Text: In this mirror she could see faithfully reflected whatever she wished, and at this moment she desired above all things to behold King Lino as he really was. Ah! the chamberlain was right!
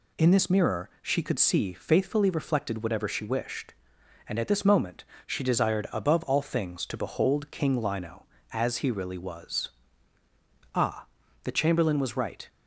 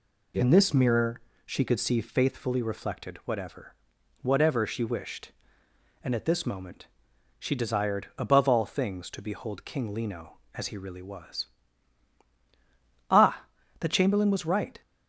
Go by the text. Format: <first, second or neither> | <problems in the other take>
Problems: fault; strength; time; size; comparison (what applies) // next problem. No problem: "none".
first | pauses between "mirror" and "she"; slight; at 1.2 s; 0.24 s long // says "whatever" twice; at 4.2 s // pauses between "moment" and "she"; noticeable; at 6.8 s; 0.52 s long; slight in the first